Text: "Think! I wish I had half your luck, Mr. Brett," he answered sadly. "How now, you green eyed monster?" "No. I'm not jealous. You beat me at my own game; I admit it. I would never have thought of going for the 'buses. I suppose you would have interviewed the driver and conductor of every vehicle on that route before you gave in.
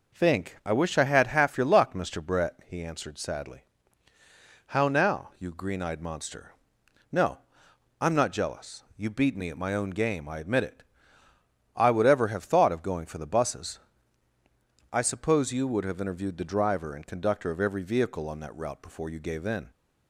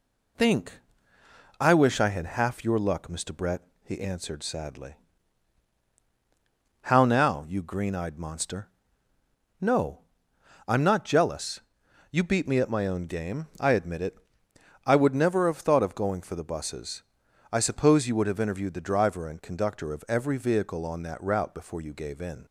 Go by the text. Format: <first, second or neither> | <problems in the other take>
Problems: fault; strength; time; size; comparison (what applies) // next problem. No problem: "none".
second | says "ever" for "never"; at 12.0 s